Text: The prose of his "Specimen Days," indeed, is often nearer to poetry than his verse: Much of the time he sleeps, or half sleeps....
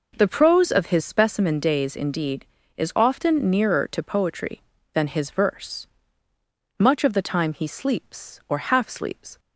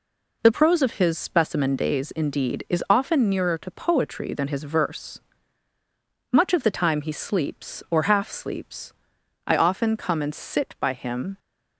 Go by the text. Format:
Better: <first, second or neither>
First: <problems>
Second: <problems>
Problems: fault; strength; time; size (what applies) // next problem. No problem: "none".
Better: first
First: none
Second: goes on to say "I often come and sit by him"; strong; from 9.4 s on; 1.9 s long